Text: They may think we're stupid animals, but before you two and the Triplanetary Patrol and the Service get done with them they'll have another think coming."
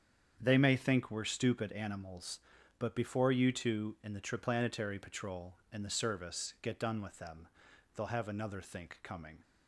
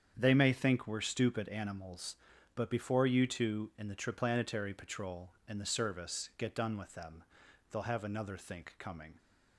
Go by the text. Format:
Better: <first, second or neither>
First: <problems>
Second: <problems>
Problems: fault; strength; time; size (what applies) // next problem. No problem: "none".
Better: neither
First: starts louder than the rest; strong; until 1.4 s; 8 dB // pauses between "them" and "they'll"; noticeable; at 7.4 s; 0.48 s long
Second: starts louder than the rest; strong; until 1.1 s; 8 dB // pauses between "them" and "they'll"; noticeable; at 7.2 s; 0.48 s long